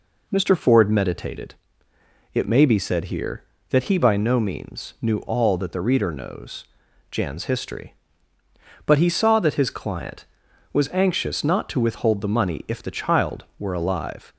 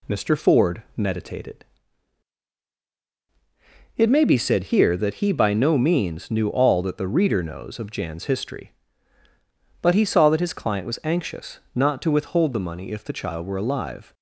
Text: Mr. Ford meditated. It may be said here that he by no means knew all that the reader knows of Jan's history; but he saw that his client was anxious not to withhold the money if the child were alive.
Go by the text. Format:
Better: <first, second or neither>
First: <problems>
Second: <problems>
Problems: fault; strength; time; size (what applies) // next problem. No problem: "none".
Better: second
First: skips "of"; at 6.8 s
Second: none